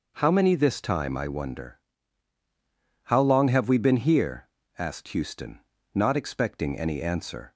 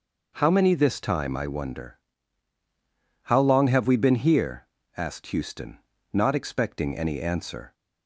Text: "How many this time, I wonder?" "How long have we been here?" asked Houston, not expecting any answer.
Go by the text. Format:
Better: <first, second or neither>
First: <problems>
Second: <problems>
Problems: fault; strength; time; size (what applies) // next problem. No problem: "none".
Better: neither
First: none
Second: none